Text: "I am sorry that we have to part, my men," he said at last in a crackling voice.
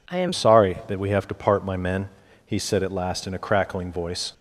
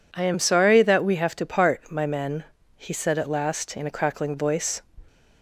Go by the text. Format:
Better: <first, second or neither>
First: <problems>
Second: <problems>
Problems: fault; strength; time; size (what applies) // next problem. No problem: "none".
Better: second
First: changes voice at "sorry"; from 0.3 s on; 4.0 s long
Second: none